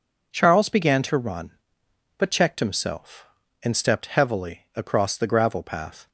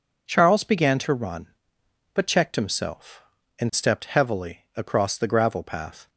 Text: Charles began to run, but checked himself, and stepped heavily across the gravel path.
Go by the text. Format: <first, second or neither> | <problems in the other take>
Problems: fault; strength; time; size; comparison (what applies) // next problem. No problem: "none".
neither | none